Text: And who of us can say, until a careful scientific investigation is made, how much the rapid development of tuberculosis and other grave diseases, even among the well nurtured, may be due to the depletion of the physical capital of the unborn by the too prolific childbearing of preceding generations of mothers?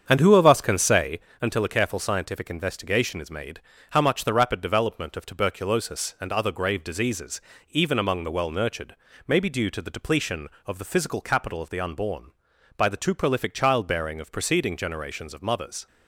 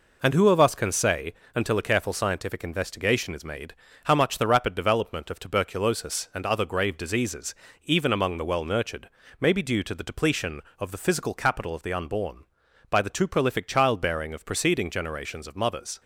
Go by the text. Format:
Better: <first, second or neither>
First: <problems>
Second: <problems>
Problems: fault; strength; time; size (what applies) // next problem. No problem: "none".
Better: second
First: starts louder than the rest; strong; until 1.2 s; 7.5 dB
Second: none